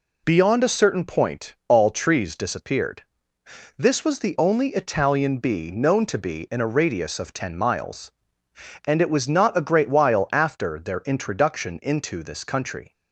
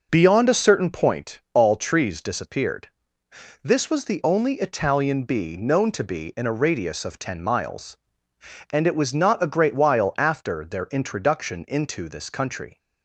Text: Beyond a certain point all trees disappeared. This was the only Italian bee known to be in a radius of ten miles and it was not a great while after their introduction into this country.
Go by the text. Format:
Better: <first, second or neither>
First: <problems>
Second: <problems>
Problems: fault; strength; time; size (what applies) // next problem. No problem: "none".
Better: first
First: none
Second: starts louder than the rest; noticeable; until 1.2 s; 5.5 dB